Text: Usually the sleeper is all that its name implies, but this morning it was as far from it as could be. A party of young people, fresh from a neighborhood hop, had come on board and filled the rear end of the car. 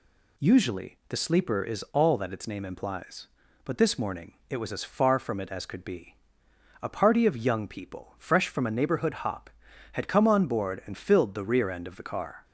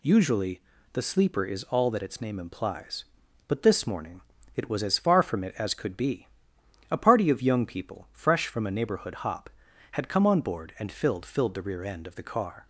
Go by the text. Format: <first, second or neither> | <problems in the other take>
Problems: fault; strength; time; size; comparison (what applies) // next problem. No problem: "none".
first | pauses between "Usually" and "the"; slight; at 0.6 s; 0.32 s long // pauses between "morning" and "it"; slight; at 4.2 s; 0.34 s long; slight in the first // says "filled" twice; at 11.2 s